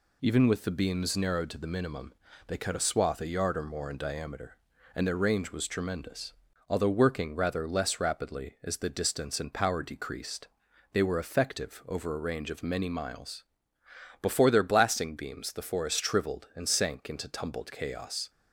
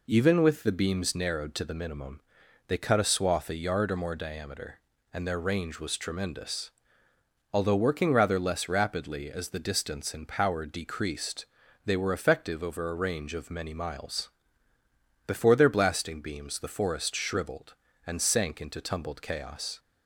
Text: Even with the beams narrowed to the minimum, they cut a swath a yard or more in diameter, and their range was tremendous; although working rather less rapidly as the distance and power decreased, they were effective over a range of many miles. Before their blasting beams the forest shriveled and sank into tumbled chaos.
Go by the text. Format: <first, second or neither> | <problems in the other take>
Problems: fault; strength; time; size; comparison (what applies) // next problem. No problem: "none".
first | skips "in"; at 4.1 s